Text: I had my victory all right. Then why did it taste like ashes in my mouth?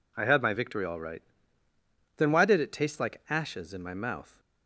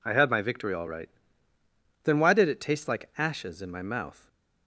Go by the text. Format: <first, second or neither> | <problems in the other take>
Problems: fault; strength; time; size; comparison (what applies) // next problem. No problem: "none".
neither | none